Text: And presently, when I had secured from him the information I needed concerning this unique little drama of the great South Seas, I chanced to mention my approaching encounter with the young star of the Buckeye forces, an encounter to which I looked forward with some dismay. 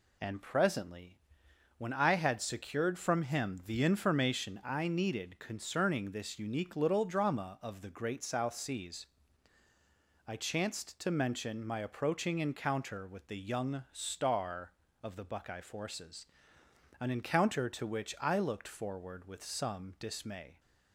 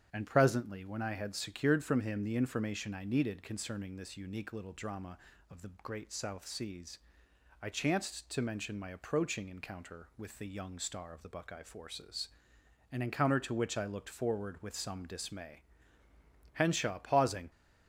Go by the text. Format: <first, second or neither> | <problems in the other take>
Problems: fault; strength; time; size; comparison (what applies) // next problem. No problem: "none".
first | starts louder than the rest; strong; until 1.1 s; 8 dB // goes on to say "Henshaw pausing"; noticeable; from 16.5 s on; 0.96 s long